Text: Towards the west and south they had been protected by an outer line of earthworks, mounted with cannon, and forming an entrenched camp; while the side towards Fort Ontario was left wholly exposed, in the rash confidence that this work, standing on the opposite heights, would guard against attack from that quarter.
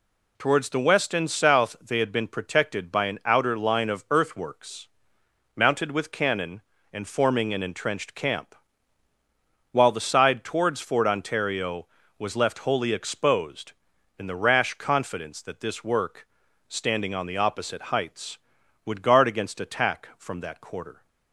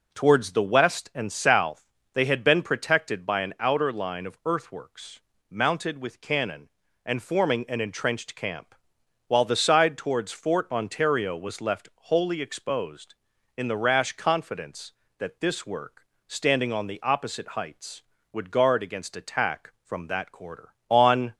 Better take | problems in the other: first | pauses between "south" and "they"; slight; at 1.8 s; 0.28 s long // goes on to say "On"; slight; from 20.8 s on; 0.46 s long

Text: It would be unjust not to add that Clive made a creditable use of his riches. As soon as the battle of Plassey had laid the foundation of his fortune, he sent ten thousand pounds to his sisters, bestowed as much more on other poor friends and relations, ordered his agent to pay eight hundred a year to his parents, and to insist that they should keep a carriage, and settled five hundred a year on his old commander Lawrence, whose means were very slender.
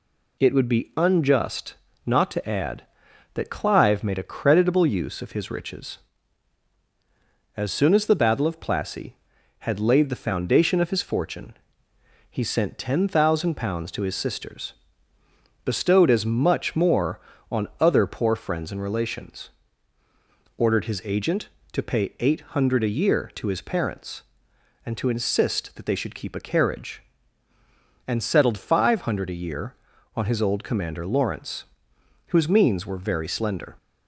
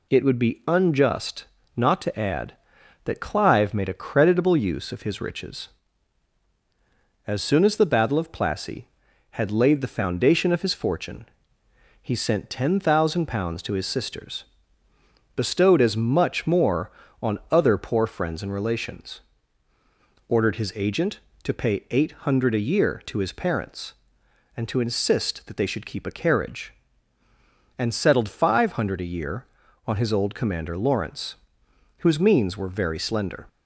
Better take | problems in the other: neither | pauses between "unjust" and "not"; slight; the same in both

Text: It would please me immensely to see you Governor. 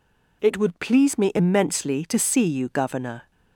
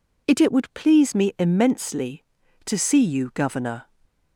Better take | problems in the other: first | says "It" twice; at 0.3 s // stays silent after the last word; slight; from 3.8 s on; 0.5 s long

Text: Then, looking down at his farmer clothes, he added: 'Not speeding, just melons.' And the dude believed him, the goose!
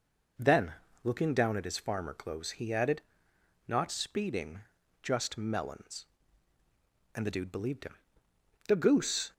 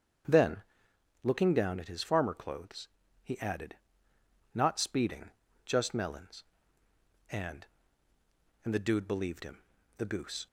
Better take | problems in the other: first | starts louder than the rest; strong; until 1.8 s; 7.5 dB // says "And" twice; at 8.6 s

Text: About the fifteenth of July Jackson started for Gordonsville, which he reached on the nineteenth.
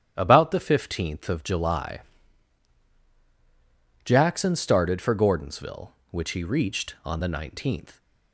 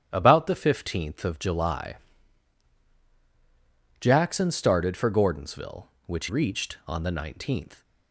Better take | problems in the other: first | starts louder than the rest; strong; until 1.1 s; 10 dB; strong in the first // pauses between "July" and "Jackson"; strong; at 1.9 s; 2.0 s long; strong in the first // skips "he"; at 6.2 s

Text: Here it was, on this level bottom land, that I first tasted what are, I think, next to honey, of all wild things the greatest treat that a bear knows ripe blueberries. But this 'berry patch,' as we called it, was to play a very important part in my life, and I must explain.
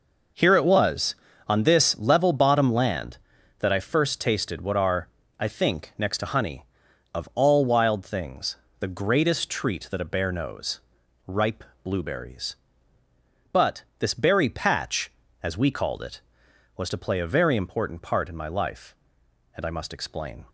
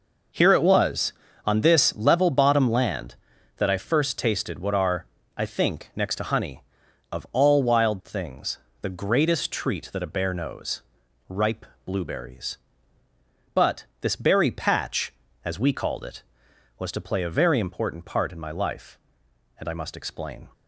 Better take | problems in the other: neither | pauses between "things" and "the"; slight; the same in both // pauses between "knows" and "ripe"; noticeable; the same in both // pauses between "ripe" and "blueberries"; slight; the same in both // pauses between "But" and "this"; slight; the same in both

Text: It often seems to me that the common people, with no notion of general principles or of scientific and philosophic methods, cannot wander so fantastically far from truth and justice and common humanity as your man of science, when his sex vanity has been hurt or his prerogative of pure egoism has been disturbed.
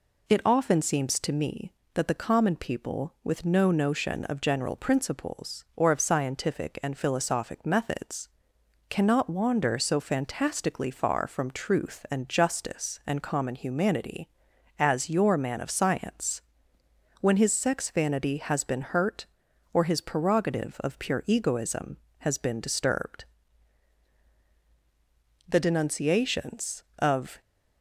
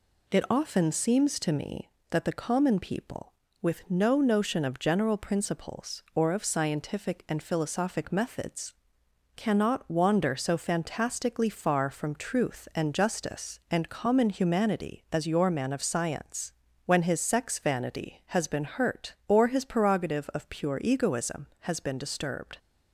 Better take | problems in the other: second | goes on to say "The denunciations of"; strong; from 25.4 s on; 1.9 s long

